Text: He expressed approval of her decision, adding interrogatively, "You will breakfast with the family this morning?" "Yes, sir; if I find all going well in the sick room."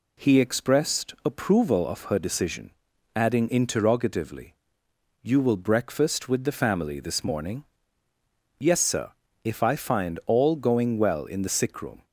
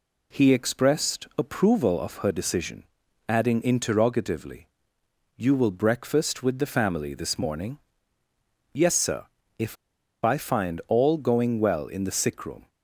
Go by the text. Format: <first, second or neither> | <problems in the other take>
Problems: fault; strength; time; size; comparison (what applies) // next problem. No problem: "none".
first | pauses between "if" and "I"; noticeable; at 9.7 s; 0.47 s long